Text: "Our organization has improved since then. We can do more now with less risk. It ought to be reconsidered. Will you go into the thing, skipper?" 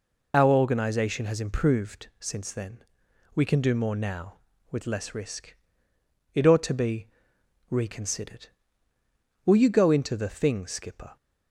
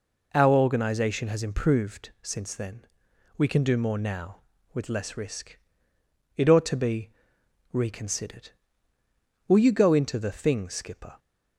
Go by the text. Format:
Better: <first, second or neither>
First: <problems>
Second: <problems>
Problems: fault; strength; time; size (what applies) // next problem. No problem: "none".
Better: second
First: loses the start of "Our"; at 0.3 s; 35 ms // pauses between "be" and "reconsidered"; noticeable; at 7.0 s; 0.62 s long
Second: pauses between "be" and "reconsidered"; noticeable; at 7.1 s; 0.62 s long